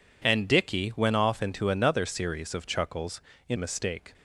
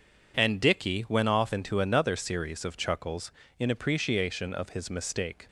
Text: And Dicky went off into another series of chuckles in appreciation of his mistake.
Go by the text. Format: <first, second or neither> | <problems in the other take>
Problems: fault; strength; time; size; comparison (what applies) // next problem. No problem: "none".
second | skips "appreciation of his"; at 3.5 s